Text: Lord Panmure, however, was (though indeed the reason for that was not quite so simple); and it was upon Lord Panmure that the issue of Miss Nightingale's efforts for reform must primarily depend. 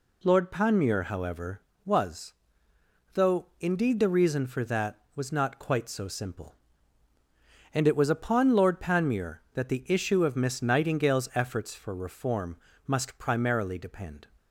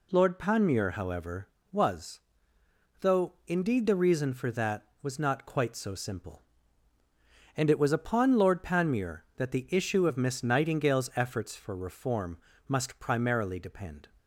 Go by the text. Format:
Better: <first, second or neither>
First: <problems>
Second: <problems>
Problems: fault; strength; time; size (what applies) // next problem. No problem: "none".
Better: neither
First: pauses between "reform" and "must"; slight; at 12.5 s; 0.30 s long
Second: pauses between "reform" and "must"; slight; at 12.3 s; 0.30 s long